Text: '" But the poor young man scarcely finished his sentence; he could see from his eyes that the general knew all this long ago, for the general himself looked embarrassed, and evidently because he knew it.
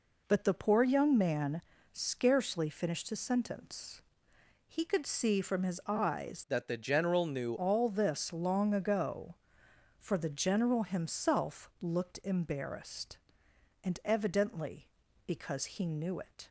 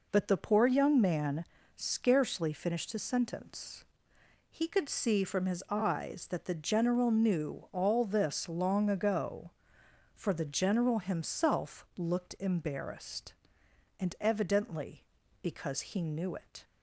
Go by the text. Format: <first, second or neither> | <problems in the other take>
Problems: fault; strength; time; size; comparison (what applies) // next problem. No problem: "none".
second | pauses between "man" and "scarcely"; slight; at 1.6 s; 0.32 s long; slight in the second // changes voice from "that" to "knew"; from 6.4 to 7.5 s; 1.1 s long